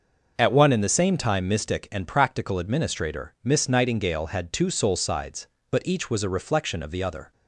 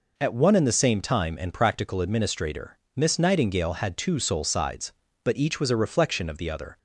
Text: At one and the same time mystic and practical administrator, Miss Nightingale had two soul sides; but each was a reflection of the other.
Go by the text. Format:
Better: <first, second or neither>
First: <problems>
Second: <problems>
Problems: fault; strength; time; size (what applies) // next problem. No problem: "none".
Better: first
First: none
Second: skips "mystic"; at 1.3 s